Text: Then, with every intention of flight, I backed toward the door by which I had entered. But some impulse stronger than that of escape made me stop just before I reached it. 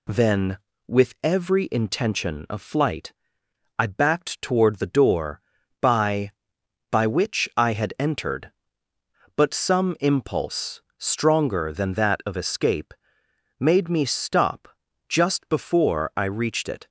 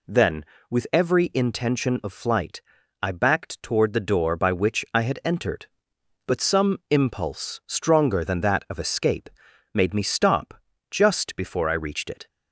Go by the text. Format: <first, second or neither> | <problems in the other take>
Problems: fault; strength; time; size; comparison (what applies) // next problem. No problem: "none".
second | says "by" twice; at 6.8 s // pauses between "impulse" and "stronger"; slight; at 10.7 s; 0.16 s long // pauses between "escape" and "made"; noticeable; at 12.9 s; 0.66 s long; noticeable in the second // pauses between "stop" and "just"; at 14.6 s; 0.42 s long; slight in the second